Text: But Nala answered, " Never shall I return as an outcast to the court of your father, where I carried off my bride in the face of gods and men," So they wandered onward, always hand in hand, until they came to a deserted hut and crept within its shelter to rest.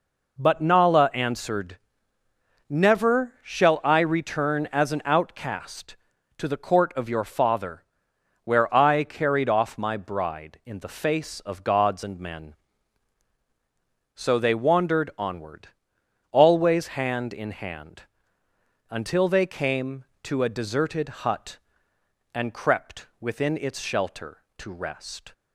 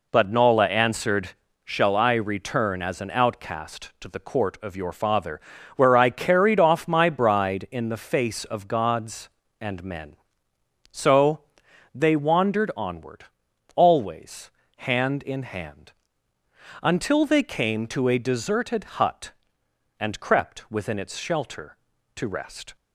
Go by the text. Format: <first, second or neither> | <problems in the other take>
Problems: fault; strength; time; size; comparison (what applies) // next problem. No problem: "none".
first | skips "Never"; at 1.6 s // pauses between "So" and "they"; noticeable; at 11.3 s; 0.52 s long // pauses between "always" and "hand"; slight; at 14.5 s; 0.26 s long // pauses between "deserted" and "hut"; slight; at 18.8 s; 0.16 s long